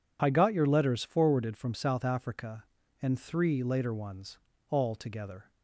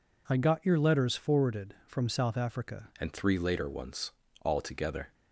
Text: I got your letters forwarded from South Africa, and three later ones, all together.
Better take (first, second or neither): first